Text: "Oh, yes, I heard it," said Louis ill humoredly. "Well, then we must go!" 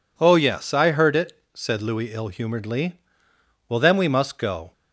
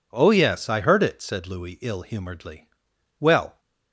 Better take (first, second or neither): first